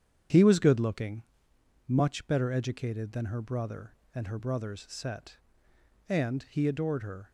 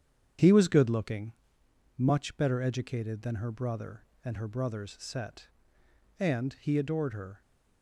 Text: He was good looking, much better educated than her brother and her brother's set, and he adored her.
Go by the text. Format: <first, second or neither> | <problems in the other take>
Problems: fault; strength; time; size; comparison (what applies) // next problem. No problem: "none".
neither | starts louder than the rest; strong; the same in both